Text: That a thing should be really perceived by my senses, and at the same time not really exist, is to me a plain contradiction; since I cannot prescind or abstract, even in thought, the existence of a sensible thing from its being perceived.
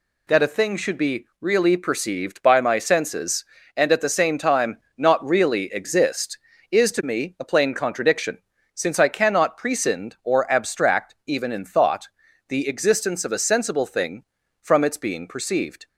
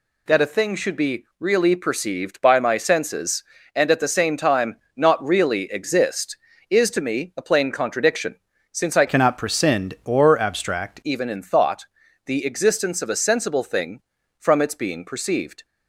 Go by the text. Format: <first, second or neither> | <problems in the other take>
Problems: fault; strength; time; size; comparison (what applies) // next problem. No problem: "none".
first | pauses between "time" and "not"; slight; at 4.7 s; 0.22 s long; slight in the first // changes voice from "cannot" to "abstract"; from 9.0 to 10.9 s; 1.9 s long